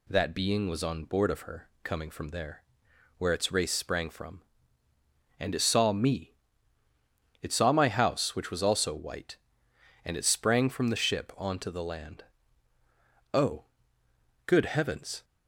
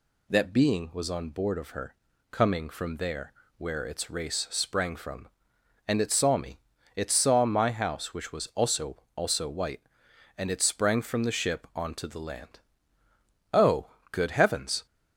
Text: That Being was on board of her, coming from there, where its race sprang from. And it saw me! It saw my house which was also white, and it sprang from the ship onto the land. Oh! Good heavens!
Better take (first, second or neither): first